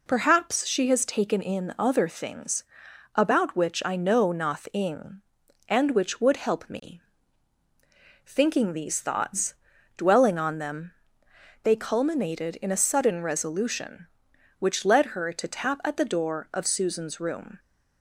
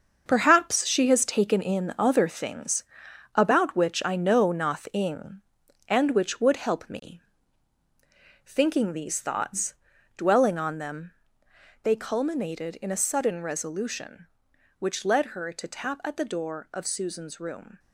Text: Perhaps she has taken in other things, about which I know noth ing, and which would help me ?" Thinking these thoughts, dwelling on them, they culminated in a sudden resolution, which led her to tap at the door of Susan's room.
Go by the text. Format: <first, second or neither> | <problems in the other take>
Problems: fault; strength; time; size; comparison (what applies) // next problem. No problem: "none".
first | gets quieter; strong; throughout; 8 dB